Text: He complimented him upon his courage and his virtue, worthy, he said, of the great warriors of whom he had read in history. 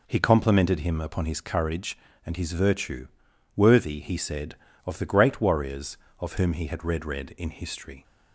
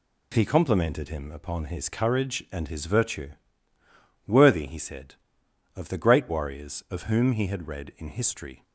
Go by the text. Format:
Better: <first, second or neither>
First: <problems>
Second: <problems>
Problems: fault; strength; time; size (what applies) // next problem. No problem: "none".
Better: second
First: says "read" twice; at 7.0 s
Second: none